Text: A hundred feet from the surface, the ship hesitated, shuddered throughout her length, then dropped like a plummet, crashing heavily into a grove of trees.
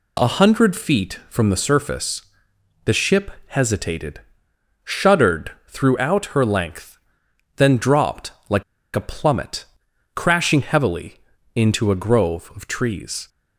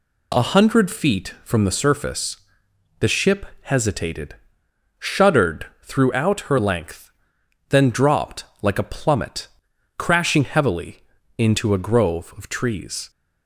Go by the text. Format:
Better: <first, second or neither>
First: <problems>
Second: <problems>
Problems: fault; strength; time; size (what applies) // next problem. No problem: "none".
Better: second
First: pauses between "ship" and "hesitated"; slight; at 3.3 s; 0.16 s long // pauses between "shuddered" and "throughout"; slight; at 5.5 s; 0.16 s long // pauses between "dropped" and "like"; slight; at 8.3 s; 0.16 s long // pauses between "like" and "a"; slight; at 8.6 s; 0.33 s long // pauses between "heavily" and "into"; at 11.1 s; 0.38 s long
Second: pauses between "ship" and "hesitated"; slight; at 3.4 s; 0.16 s long // pauses between "shuddered" and "throughout"; slight; at 5.6 s; 0.16 s long // pauses between "dropped" and "like"; slight; at 8.4 s; 0.16 s long // pauses between "heavily" and "into"; at 10.9 s; 0.38 s long